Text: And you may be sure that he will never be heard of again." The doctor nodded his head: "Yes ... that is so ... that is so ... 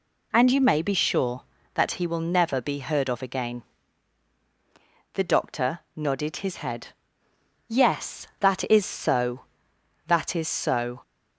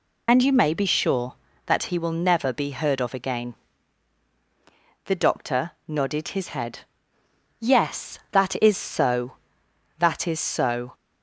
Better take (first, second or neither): first